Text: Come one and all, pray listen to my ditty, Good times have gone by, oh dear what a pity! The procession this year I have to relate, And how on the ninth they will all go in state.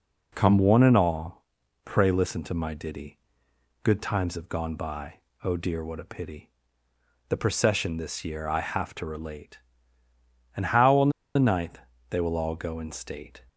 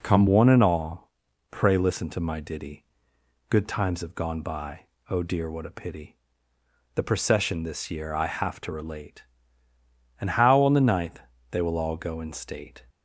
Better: second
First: pauses between "on" and "the"; slight; at 11.0 s; 0.25 s long // pauses between "ninth" and "they"; slight; at 11.7 s; 0.30 s long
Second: pauses between "ninth" and "they"; slight; at 11.1 s; 0.30 s long

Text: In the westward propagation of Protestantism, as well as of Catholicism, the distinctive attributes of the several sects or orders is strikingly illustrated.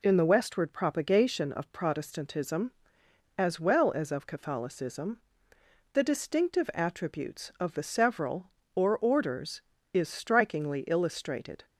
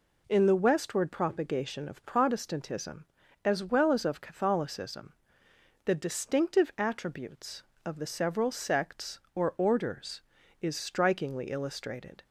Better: second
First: skips "sects"; at 8.6 s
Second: none

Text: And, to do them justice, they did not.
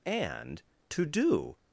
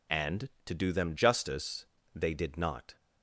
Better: second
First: stops before "them justice they did not"; at 1.5 s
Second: none

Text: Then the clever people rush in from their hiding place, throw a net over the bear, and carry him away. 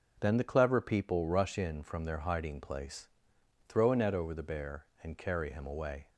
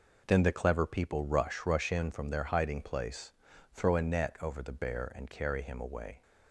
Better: first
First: none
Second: says "rush" twice; at 1.6 s

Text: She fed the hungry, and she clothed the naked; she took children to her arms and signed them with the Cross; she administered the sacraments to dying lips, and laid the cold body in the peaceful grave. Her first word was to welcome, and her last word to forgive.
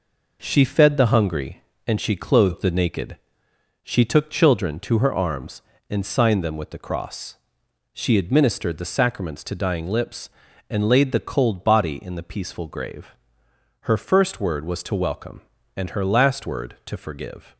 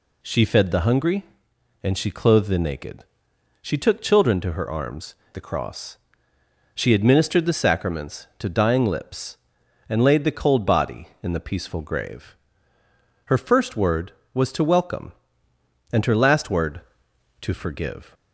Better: first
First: none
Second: skips "and signed them with"; at 5.2 s

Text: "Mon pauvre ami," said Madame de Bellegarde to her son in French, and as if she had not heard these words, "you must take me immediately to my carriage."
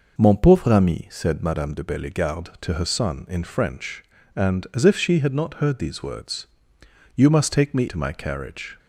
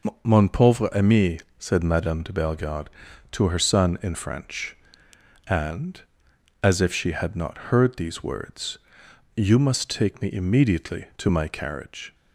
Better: second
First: skips "immediately"; at 7.8 s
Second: none

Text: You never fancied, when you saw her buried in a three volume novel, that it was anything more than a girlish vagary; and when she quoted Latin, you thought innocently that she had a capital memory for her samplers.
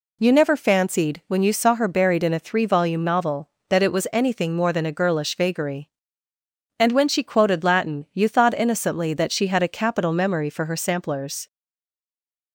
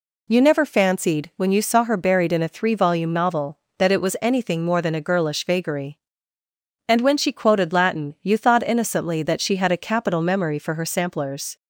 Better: second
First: stays silent after the last word; from 11.4 s on; 1.1 s long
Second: none

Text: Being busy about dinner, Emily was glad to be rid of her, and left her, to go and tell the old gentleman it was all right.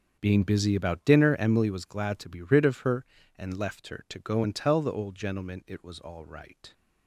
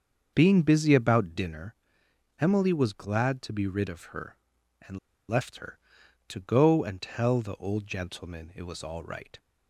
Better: first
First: starts louder than the rest; until 1.2 s; 6.5 dB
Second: starts louder than the rest; until 1.3 s; 6.5 dB // pauses between "and" and "left"; slight; at 4.9 s; 0.30 s long

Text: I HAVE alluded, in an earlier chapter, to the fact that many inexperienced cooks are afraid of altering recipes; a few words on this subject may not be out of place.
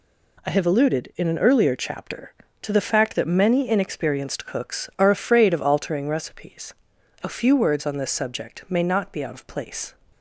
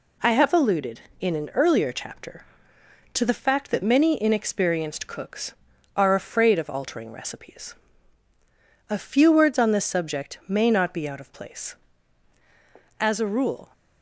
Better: first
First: none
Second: goes on to say "As a rule"; noticeable; from 12.9 s on; 0.70 s long

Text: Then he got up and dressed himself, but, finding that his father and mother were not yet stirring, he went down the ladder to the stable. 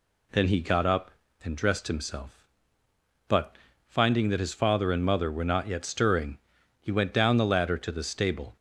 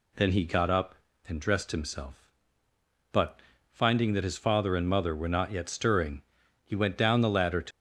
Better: first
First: none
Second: stops before "the stable"; at 7.7 s

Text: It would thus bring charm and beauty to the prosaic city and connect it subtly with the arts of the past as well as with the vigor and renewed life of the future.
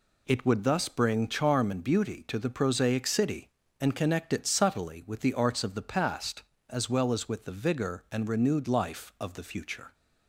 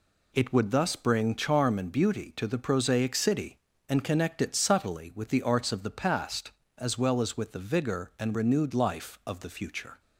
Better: neither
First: none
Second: none

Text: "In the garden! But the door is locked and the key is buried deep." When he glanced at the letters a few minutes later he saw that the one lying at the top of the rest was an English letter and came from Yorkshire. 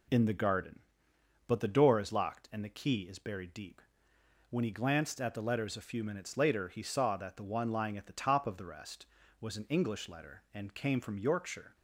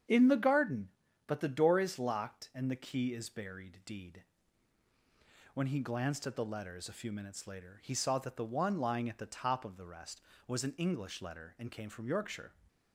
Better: first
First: none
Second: starts louder than the rest; strong; until 1.4 s; 8 dB // says "deed" for "deep"; at 3.8 s

